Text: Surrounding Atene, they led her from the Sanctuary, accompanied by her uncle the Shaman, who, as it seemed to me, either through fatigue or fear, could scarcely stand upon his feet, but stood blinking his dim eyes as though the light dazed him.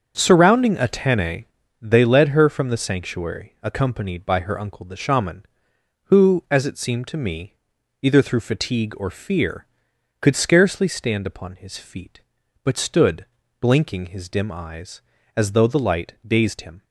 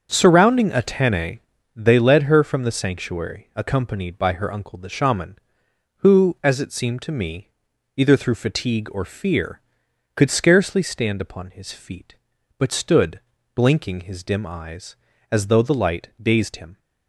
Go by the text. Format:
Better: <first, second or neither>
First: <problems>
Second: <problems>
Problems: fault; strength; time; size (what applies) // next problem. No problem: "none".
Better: neither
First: starts louder than the rest; until 1.1 s; 6.5 dB // pauses between "stood" and "blinking"; slight; at 13.2 s; 0.32 s long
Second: starts louder than the rest; until 1.1 s; 6.5 dB // pauses between "stood" and "blinking"; slight; at 13.2 s; 0.32 s long